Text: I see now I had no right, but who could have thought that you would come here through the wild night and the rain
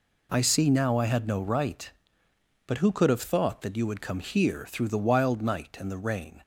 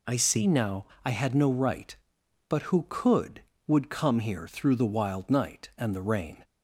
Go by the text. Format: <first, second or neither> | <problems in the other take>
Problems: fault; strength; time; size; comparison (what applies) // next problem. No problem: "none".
first | pauses between "now" and "I"; slight; at 0.8 s; 0.18 s long // skips "have thought that you"; at 3.5 s